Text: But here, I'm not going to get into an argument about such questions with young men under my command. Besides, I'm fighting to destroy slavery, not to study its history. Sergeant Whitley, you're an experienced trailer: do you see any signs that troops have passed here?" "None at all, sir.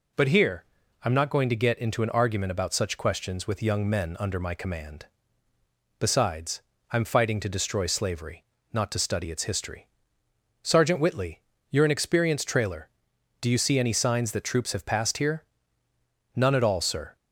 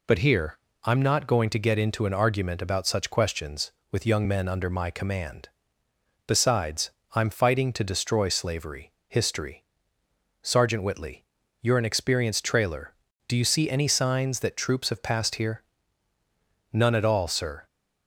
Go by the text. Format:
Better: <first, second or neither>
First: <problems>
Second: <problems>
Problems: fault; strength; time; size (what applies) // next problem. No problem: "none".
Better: first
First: none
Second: skips "not to study its"; at 8.9 s